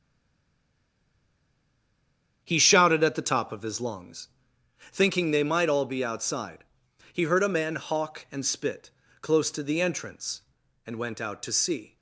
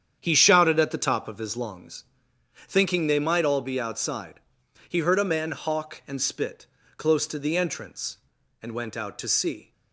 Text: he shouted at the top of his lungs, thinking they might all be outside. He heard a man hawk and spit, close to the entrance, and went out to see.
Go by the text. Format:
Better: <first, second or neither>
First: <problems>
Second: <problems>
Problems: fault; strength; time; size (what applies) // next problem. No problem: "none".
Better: second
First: stays silent before the first word; until 2.4 s; 2.4 s long // starts louder than the rest; strong; until 3.4 s; 8.5 dB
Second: starts louder than the rest; strong; until 1.2 s; 8.5 dB